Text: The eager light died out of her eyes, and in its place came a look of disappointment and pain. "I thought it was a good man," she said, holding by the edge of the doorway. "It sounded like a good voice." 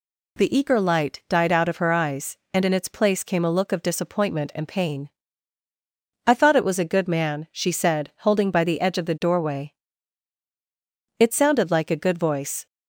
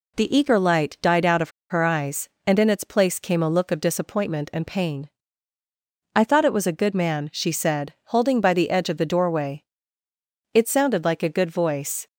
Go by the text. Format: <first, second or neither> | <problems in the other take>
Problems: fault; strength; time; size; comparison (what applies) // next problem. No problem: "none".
first | pauses between "of" and "her"; slight; at 1.4 s; 0.20 s long